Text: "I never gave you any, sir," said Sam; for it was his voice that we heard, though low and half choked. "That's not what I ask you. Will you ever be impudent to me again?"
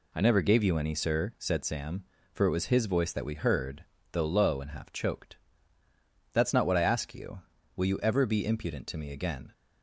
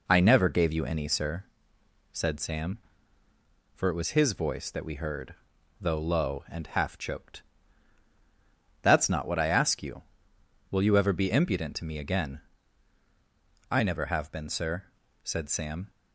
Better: first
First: none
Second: goes on to say "I never have been sir said Sam"; strong; from 13.6 s on; 2.2 s long

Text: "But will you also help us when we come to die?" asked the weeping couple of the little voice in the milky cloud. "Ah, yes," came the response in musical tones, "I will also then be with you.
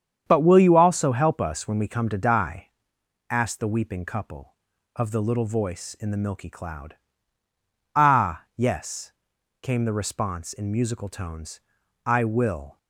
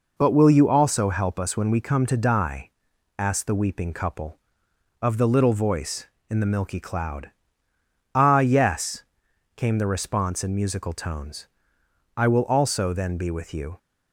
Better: second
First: starts louder than the rest; strong; until 1.2 s; 8 dB // stops before "also then be with you"; at 12.7 s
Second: none

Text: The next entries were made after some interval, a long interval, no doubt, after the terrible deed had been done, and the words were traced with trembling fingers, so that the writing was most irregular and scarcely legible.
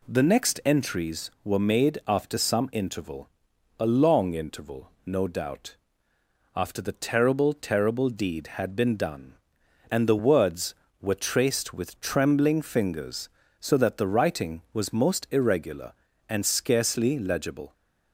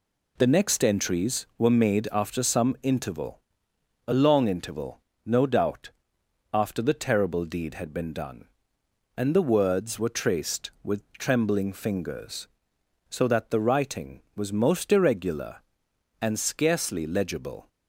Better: second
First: says "terrible" twice; at 7.5 s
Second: none

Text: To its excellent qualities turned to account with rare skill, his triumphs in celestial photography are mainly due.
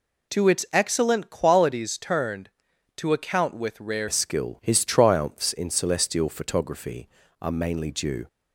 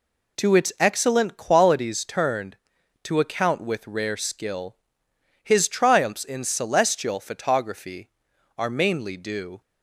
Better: second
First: changes voice at "skill"; from 4.0 s on; 4.2 s long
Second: none

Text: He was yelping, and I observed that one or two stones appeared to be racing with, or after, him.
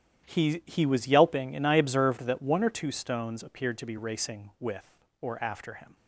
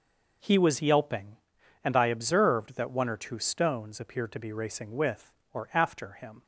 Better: second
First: starts louder than the rest; strong; until 1.2 s; 11 dB // says "He" twice; at 0.6 s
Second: none

